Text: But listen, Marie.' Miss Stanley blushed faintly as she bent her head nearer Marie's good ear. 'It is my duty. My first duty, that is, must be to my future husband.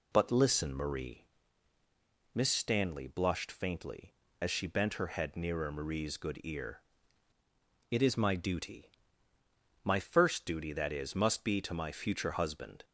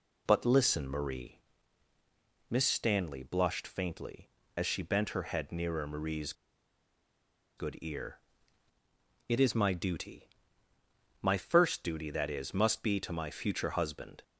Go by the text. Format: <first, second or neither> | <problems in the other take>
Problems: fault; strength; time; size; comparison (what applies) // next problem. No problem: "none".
first | pauses between "Marie's" and "good"; strong; at 6.3 s; 1.2 s long